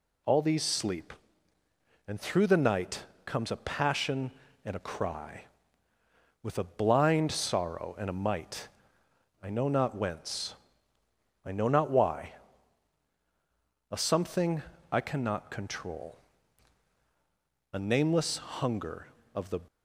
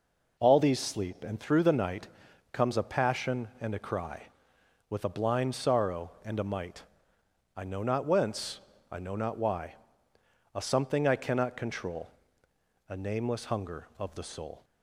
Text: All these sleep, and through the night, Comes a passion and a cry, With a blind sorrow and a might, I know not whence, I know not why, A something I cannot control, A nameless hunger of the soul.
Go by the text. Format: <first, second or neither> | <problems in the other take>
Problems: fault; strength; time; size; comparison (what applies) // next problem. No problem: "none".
second | pauses between "something" and "I"; slight; at 14.6 s; 0.30 s long // stops before "soul"; at 19.6 s